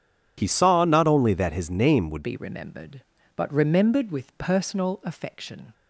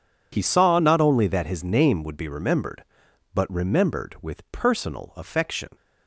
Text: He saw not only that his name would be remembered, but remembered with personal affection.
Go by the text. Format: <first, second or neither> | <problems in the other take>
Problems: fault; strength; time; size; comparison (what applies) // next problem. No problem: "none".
second | changes voice at "be"; from 2.2 s on; 3.5 s long